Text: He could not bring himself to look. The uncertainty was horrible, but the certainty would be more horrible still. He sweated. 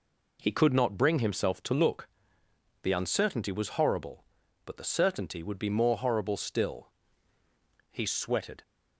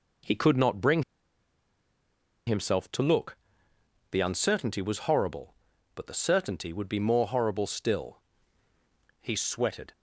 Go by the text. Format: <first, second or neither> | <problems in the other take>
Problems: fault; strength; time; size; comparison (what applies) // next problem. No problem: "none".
first | pauses between "bring" and "himself"; strong; at 1.0 s; 1.4 s long